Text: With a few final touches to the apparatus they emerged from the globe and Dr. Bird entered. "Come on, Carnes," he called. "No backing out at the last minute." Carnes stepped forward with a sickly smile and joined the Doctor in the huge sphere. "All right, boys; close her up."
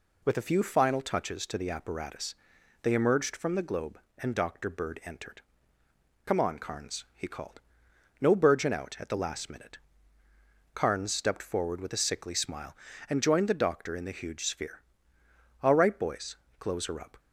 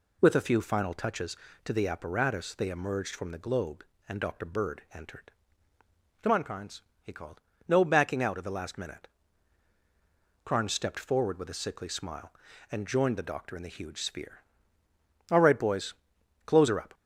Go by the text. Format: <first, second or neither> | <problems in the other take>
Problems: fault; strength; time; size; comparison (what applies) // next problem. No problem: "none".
second | pauses between "apparatus" and "they"; noticeable; at 2.3 s; 0.48 s long // says "burgeon" for "backing"; at 8.3 s